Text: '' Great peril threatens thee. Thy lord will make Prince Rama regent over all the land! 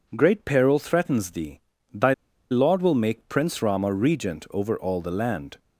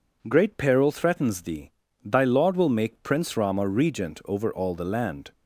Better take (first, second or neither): second